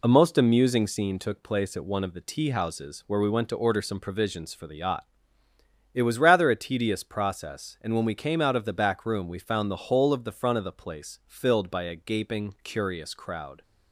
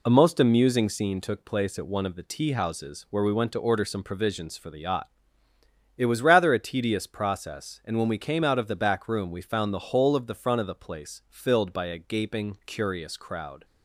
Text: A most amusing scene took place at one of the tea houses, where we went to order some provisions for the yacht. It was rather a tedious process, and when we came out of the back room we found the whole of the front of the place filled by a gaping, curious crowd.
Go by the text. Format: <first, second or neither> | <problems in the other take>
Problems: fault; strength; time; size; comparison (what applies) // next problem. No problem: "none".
neither | none